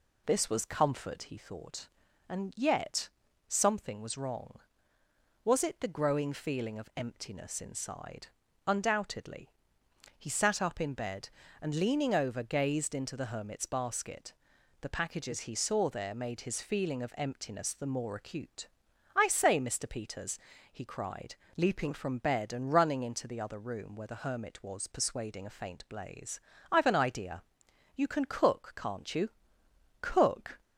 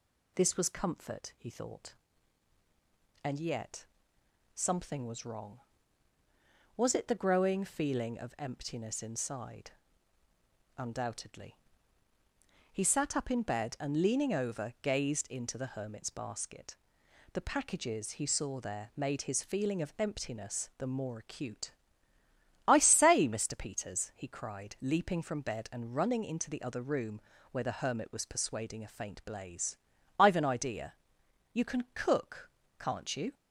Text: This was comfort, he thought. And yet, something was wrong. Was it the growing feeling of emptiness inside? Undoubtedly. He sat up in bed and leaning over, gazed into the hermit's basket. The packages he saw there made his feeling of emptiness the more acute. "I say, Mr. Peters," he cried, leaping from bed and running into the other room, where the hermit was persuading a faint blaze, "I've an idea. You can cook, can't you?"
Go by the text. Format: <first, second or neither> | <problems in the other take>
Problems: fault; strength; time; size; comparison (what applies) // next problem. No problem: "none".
second | goes on to say "Cook"; from 30.0 s on; 0.60 s long